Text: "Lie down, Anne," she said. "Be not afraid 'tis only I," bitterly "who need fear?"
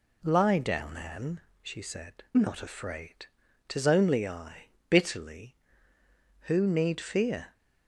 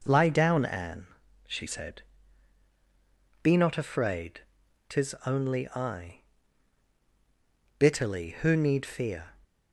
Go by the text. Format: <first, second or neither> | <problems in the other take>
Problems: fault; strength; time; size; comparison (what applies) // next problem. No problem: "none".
second | skips "Be"; at 2.2 s // pauses between "afraid" and "tis"; at 3.2 s; 0.40 s long; noticeable in the second